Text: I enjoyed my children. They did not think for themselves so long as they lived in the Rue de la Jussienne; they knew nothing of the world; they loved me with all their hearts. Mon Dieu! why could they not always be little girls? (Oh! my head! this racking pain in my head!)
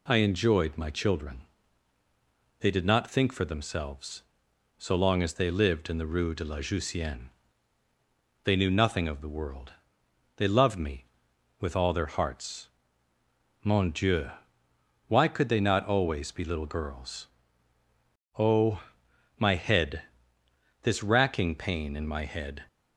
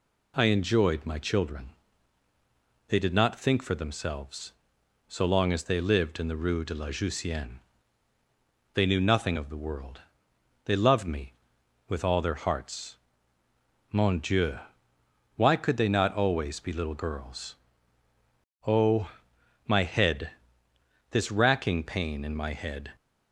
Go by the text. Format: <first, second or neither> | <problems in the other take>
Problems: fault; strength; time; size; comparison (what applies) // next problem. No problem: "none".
neither | none